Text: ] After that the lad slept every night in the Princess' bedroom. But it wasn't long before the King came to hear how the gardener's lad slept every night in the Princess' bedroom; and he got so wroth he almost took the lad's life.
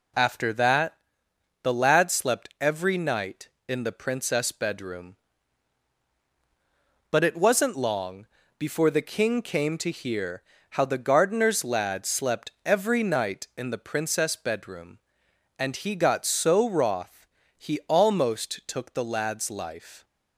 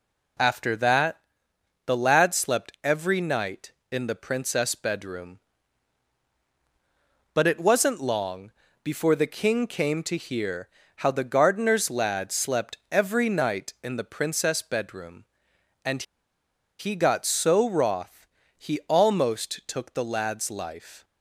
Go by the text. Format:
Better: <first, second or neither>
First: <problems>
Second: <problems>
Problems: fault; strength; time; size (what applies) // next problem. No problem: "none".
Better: first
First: pauses between "that" and "the"; noticeable; at 0.9 s; 0.68 s long // pauses between "long" and "before"; slight; at 8.2 s; 0.32 s long // pauses between "hear" and "how"; slight; at 10.4 s; 0.28 s long // pauses between "slept" and "every"; slight; at 12.4 s; 0.16 s long // pauses between "wroth" and "he"; slight; at 17.2 s; 0.32 s long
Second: pauses between "that" and "the"; noticeable; at 1.1 s; 0.68 s long // pauses between "long" and "before"; slight; at 8.5 s; 0.32 s long // pauses between "hear" and "how"; slight; at 10.6 s; 0.28 s long // pauses between "slept" and "every"; slight; at 12.7 s; 0.16 s long // pauses between "and" and "he"; noticeable; at 16.0 s; 0.75 s long // pauses between "wroth" and "he"; slight; at 18.2 s; 0.32 s long